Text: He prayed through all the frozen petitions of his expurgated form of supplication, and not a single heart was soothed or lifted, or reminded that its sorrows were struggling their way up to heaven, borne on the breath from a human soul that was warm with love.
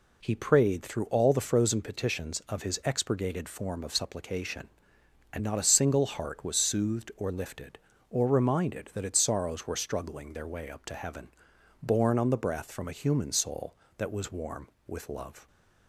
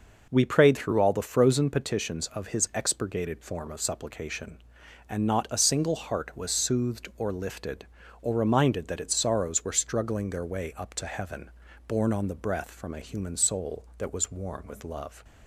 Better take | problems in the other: first | says "We" for "He"; at 0.2 s

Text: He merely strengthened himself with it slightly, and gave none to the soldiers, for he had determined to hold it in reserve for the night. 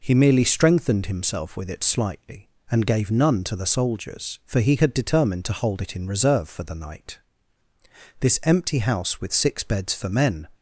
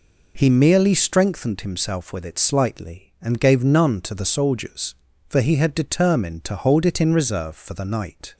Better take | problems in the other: second | goes on to say "This empty house with six beds for men"; strong; from 8.1 s on; 2.3 s long

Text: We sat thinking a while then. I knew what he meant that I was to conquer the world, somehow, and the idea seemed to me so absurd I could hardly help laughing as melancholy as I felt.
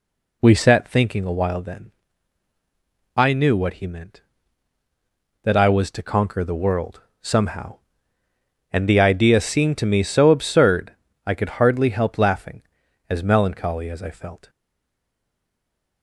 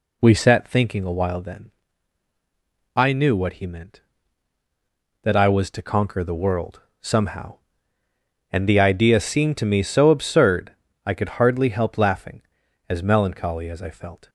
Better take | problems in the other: second | pauses between "absurd" and "I"; slight; at 10.9 s; 0.32 s long; slight in the second // stays silent after the last word; noticeable; from 14.4 s on; 1.6 s long

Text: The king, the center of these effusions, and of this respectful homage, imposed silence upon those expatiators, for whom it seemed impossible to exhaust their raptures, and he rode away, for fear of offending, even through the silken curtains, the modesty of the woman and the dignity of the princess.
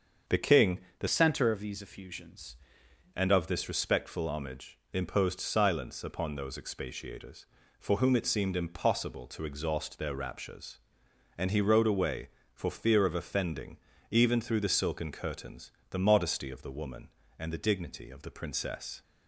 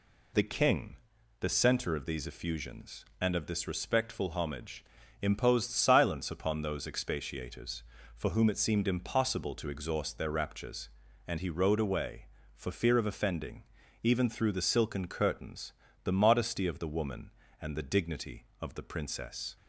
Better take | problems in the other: second | starts louder than the rest; until 1.4 s; 7 dB // changes voice from "center" to "effusions"; from 1.0 to 2.5 s; 1.5 s long

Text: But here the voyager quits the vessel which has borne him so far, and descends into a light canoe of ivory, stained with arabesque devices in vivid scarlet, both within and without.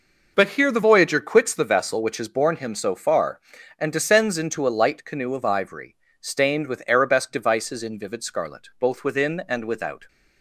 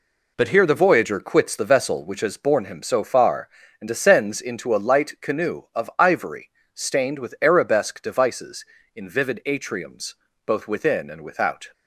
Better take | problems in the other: first | says "atriums" for "scarlet"; at 9.4 s

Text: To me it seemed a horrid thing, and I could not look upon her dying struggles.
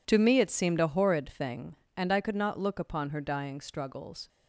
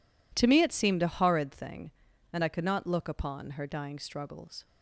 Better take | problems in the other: neither | none

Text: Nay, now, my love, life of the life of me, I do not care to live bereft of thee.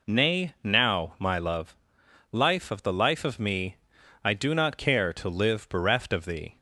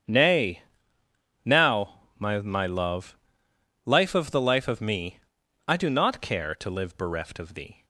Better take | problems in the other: first | starts louder than the rest; strong; until 1.8 s; 8.5 dB // says "my" twice; at 2.4 s

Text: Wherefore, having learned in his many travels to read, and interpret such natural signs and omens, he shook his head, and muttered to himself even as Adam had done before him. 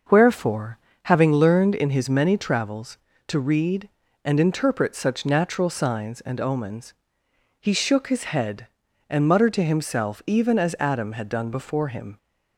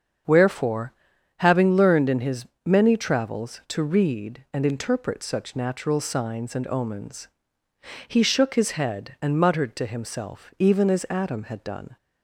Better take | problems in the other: first | starts louder than the rest; strong; until 1.7 s; 7 dB; noticeable in the first // pauses between "his" and "many"; slight; at 2.4 s; 0.18 s long // stops before "before him"; at 11.9 s

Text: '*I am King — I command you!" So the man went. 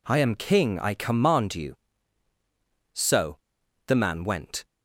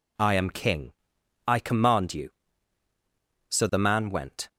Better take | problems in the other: second | pauses between "So" and "the"; noticeable; at 3.3 s; 0.51 s long

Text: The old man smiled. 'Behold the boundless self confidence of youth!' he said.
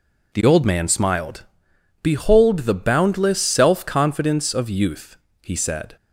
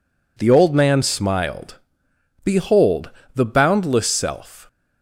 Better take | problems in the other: first | pauses between "Behold" and "the"; slight; at 3.0 s; 0.26 s long // stops before "confidence of youth he said"; at 4.6 s

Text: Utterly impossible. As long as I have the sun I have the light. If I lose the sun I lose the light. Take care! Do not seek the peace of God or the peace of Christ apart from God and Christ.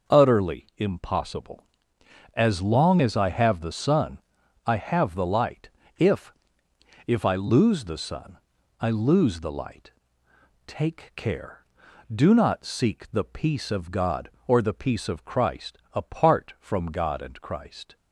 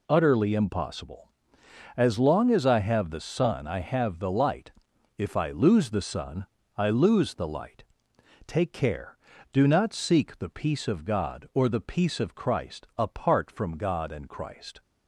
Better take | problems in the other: second | pauses between "sun" and "I"; at 4.1 s; 0.44 s long // says "If" twice; at 7.0 s // pauses between "sun" and "I"; at 8.3 s; 0.42 s long; slight in the second // pauses between "Christ" and "apart"; slight; at 15.7 s; 0.16 s long

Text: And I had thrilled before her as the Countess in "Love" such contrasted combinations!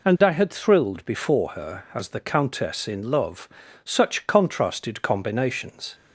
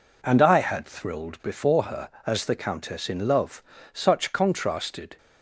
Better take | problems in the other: first | pauses between "Love" and "such"; slight; at 3.6 s; 0.32 s long; also in the first // stops before "combinations"; at 5.1 s

